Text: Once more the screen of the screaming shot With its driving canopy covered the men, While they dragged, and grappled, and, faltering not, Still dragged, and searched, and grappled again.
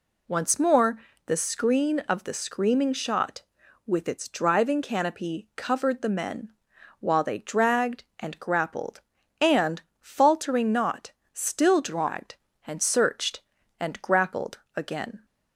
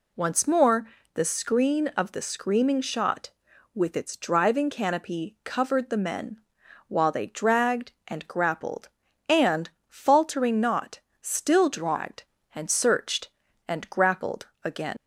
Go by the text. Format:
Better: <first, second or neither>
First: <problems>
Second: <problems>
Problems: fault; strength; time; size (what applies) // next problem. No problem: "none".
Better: first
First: pauses between "more" and "the"; slight; at 0.9 s; 0.28 s long // pauses between "grappled" and "again"; slight; at 14.5 s; 0.18 s long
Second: pauses between "more" and "the"; slight; at 0.8 s; 0.28 s long // pauses between "grappled" and "again"; slight; at 14.4 s; 0.18 s long // leaves "again" unfinished; at 14.9 s; 160 ms